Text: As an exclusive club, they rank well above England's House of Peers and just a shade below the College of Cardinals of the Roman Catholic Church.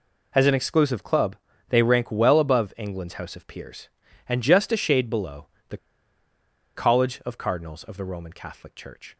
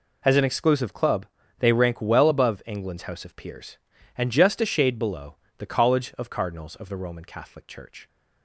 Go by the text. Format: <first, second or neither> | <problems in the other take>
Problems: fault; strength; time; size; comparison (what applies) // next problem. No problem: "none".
second | pauses between "below" and "the"; slight; at 5.4 s; 0.22 s long; slight in the second // pauses between "the" and "College"; at 5.7 s; 0.98 s long